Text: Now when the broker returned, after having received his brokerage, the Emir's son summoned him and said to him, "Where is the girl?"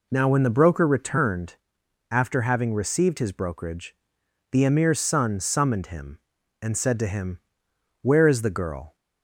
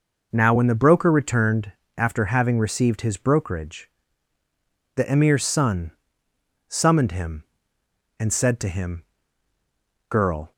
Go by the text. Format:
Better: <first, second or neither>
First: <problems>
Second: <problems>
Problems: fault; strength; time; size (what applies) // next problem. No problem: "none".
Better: first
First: none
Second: pauses between "son" and "summoned"; noticeable; at 5.9 s; 0.76 s long // skips "Where is the"; at 9.5 s